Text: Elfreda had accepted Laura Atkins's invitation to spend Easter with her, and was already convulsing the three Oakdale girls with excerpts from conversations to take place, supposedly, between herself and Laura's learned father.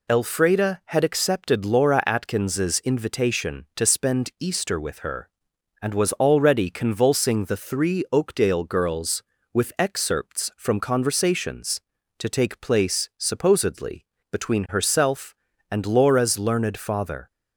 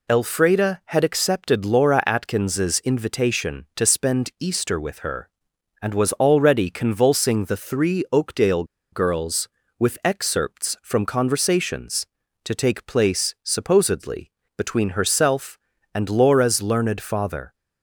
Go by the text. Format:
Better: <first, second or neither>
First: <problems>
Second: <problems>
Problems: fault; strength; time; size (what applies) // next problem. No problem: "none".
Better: first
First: none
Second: pauses between "Oakdale" and "girls"; slight; at 8.6 s; 0.27 s long